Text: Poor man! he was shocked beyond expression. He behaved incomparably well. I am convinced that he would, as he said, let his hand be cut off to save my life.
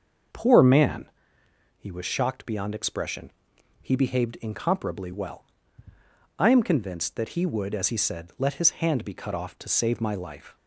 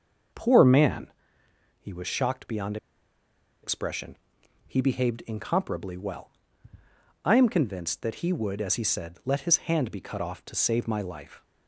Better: first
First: starts louder than the rest; until 2.0 s; 6 dB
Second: starts louder than the rest; until 2.0 s; 6 dB // pauses between "beyond" and "expression"; noticeable; at 2.7 s; 0.86 s long

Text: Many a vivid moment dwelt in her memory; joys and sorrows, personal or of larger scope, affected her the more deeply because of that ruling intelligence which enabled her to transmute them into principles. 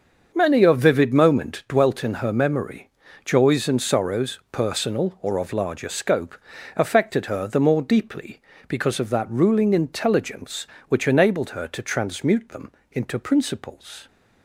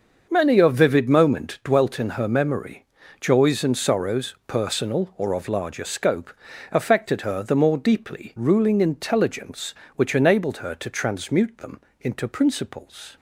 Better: first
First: starts louder than the rest; until 1.3 s; 6.5 dB // pauses between "them" and "into"; slight; at 12.7 s; 0.22 s long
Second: starts louder than the rest; until 1.3 s; 6.5 dB // skips "because of that"; at 8.3 s // pauses between "them" and "into"; slight; at 11.7 s; 0.22 s long

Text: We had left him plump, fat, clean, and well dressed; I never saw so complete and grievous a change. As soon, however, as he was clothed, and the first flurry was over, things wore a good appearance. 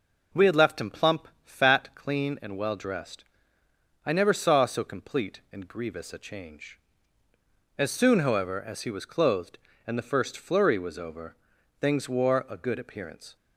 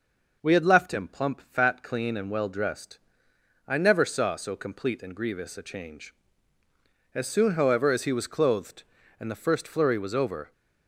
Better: first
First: none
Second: stops before "things wore a good appearance"; at 10.5 s

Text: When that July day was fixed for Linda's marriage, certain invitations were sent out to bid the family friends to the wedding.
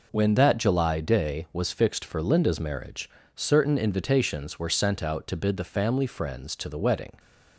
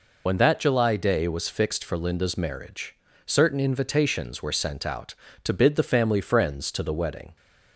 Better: first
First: none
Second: loses the start of "When"; at 0.2 s; 60 ms

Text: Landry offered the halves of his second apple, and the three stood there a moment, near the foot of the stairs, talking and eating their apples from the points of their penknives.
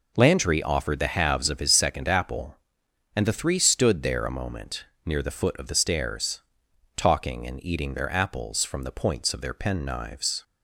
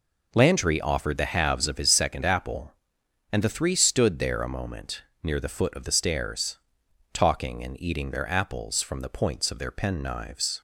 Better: neither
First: none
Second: none

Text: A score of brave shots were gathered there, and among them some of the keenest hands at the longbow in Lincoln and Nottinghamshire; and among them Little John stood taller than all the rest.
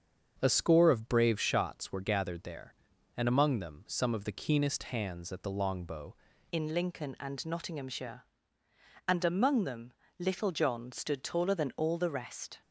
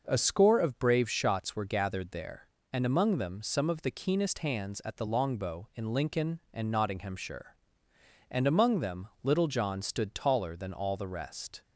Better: second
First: starts louder than the rest; until 1.4 s; 7 dB // changes voice at "in"; from 6.5 s on; 6.1 s long // pauses between "them" and "Little"; slight; at 9.9 s; 0.26 s long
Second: none

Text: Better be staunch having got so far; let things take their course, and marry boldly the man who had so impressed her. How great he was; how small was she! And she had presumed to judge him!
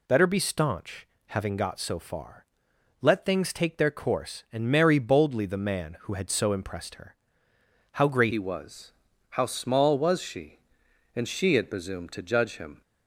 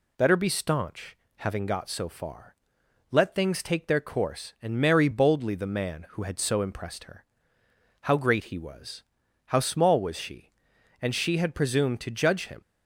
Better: second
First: pauses between "staunch" and "having"; slight; at 1.0 s; 0.22 s long // changes voice at "he"; from 8.3 s on; 4.5 s long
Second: pauses between "staunch" and "having"; slight; at 1.1 s; 0.22 s long

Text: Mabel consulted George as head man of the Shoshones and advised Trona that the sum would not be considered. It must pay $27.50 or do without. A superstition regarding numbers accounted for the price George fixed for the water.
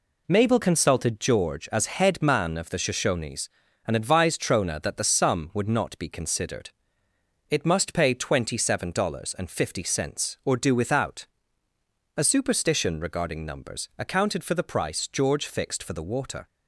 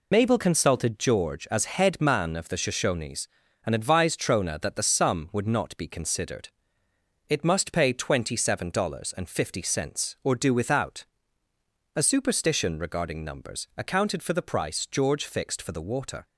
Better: first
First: none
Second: loses the start of "Mabel"; at 0.1 s; 65 ms

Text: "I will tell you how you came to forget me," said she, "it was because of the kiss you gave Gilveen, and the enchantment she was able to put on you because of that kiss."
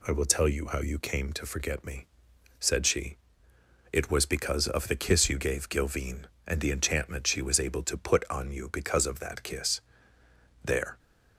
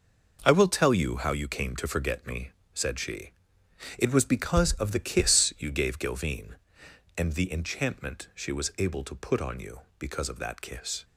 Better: second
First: goes on to say "There"; slight; from 10.6 s on; 0.34 s long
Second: none

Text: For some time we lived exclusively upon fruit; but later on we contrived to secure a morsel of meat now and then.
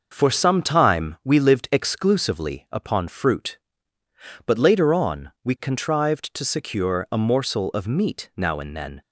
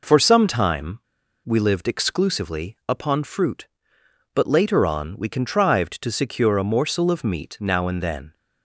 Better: first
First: none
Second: pauses between "time" and "we"; noticeable; at 0.9 s; 0.47 s long

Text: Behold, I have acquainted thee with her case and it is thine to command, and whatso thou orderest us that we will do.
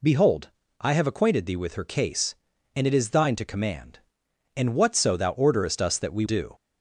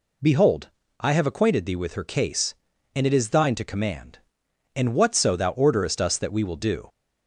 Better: second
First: skips "will"; at 6.2 s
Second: none

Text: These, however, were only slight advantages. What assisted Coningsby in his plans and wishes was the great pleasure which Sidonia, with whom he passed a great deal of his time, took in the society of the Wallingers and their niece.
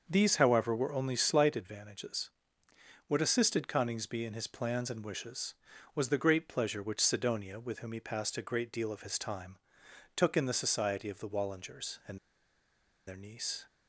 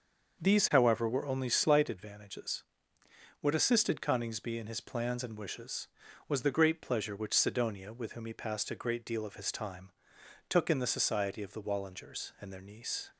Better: second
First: starts louder than the rest; until 1.0 s; 6.5 dB // pauses between "and" and "their"; noticeable; at 12.1 s; 0.88 s long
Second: starts louder than the rest; until 1.4 s; 6.5 dB

